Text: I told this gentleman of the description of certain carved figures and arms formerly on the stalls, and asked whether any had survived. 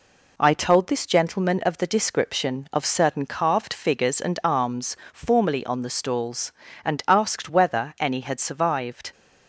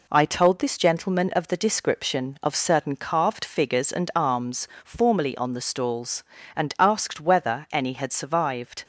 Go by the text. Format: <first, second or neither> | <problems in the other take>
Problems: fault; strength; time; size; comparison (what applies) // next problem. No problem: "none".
neither | pauses between "arms" and "formerly"; slight; the same in both